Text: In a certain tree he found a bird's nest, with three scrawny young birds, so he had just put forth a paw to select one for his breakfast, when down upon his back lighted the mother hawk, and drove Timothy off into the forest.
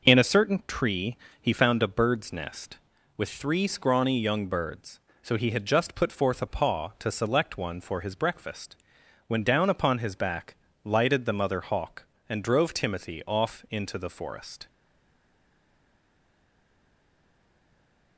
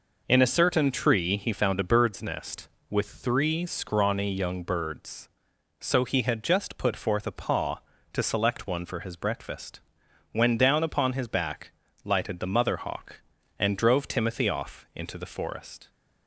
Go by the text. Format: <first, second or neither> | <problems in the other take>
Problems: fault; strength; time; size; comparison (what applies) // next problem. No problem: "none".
second | pauses between "tree" and "he"; slight; at 1.1 s; 0.26 s long // pauses between "back" and "lighted"; slight; at 10.5 s; 0.28 s long; slight in the second // stays silent after the last word; strong; from 14.6 s on; 3.5 s long